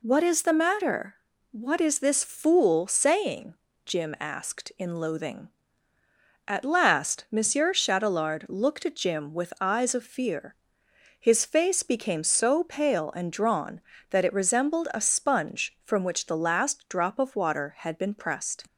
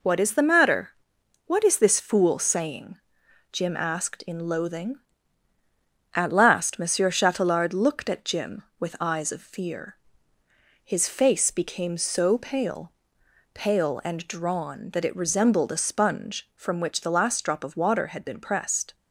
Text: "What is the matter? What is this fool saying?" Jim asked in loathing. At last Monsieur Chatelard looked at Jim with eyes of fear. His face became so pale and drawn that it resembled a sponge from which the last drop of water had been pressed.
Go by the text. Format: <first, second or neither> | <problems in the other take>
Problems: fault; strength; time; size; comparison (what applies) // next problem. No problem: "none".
first | says "pale" twice; at 13.5 s